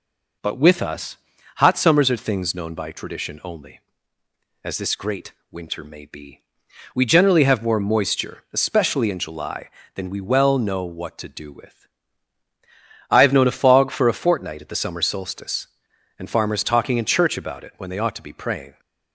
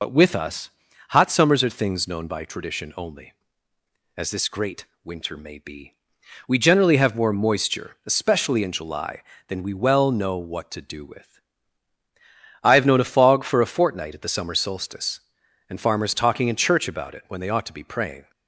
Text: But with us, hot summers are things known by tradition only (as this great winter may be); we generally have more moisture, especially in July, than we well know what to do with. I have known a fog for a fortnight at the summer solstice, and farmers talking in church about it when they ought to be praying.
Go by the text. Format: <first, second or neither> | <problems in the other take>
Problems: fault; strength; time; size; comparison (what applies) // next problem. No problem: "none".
first | loses the start of "But"; at 0.0 s; 60 ms // pauses between "great" and "winter"; slight; at 4.8 s; 0.18 s long; slight in the first